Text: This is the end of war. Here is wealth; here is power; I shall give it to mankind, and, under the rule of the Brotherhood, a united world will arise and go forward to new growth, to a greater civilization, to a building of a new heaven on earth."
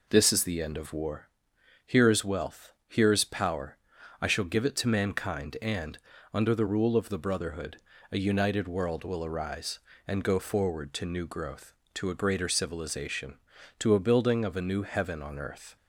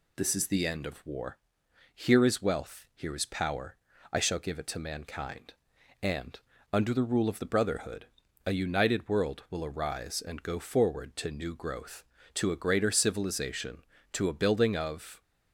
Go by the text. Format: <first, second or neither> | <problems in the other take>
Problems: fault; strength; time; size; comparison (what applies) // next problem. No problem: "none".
first | stops before "a new heaven on earth"; at 15.2 s